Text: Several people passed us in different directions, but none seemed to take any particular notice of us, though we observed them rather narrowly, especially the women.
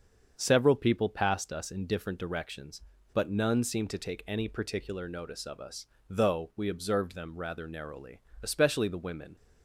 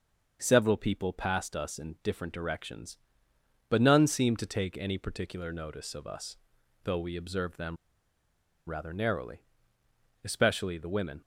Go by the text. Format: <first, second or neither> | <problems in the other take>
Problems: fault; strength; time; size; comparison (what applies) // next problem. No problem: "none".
first | starts louder than the rest; until 1.4 s; 6 dB; also in the first // pauses between "them" and "rather"; noticeable; at 7.7 s; 0.92 s long